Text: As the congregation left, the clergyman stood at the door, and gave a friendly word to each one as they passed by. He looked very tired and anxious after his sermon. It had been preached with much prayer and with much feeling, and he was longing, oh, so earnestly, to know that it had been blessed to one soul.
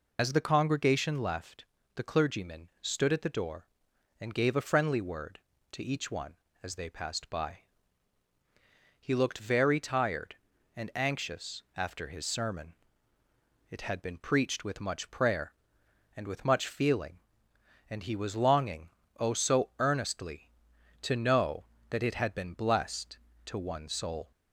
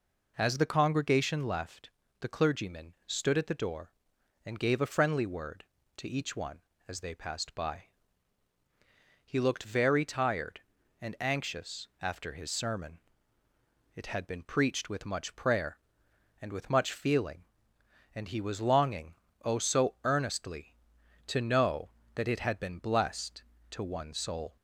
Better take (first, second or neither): second